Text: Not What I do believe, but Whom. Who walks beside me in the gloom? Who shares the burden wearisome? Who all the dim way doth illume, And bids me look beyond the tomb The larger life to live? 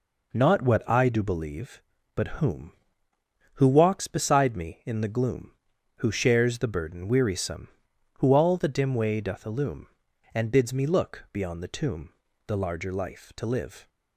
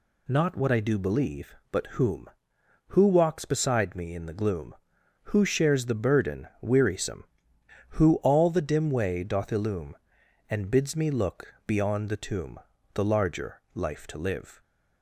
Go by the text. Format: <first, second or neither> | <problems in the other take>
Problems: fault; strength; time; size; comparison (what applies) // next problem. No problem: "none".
neither | pauses between "tomb" and "The"; slight; the same in both